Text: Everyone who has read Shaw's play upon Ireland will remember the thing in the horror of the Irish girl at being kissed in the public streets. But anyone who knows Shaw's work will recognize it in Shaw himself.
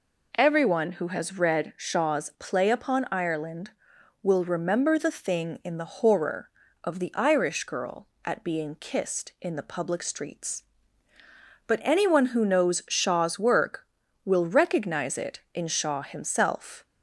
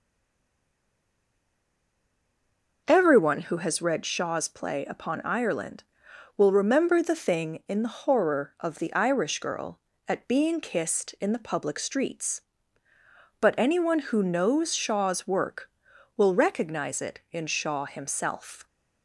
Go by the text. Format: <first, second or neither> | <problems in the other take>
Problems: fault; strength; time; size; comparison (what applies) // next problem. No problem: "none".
first | stays silent before the first word; strong; until 2.8 s; 2.8 s long